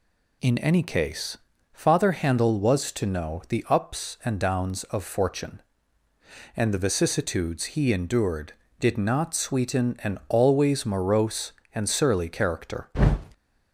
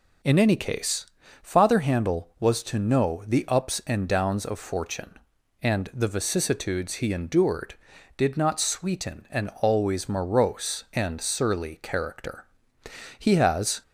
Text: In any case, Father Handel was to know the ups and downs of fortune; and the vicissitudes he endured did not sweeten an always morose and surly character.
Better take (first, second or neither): first